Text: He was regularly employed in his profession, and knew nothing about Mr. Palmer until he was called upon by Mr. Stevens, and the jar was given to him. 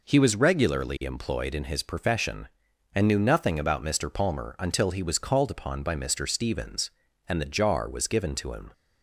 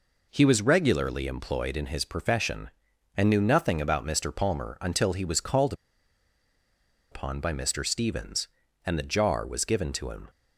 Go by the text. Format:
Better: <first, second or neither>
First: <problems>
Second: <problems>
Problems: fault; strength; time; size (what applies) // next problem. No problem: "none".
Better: first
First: none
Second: pauses between "called" and "upon"; strong; at 5.7 s; 1.3 s long